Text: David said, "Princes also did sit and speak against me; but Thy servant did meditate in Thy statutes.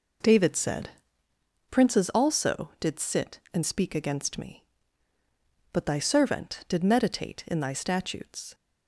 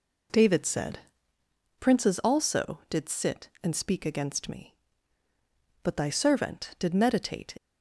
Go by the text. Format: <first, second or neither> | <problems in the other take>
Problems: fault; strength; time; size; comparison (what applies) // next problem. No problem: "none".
first | stops before "in Thy statutes"; at 7.5 s